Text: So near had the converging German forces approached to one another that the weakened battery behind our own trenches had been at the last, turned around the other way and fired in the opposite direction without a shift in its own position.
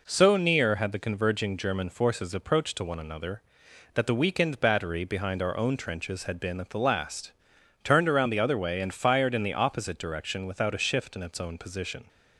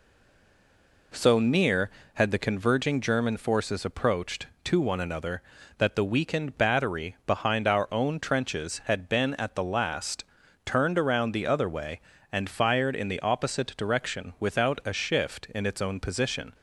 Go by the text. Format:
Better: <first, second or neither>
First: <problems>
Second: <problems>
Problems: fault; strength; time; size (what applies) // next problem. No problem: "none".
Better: first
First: none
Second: stays silent before the first word; until 1.1 s; 1.1 s long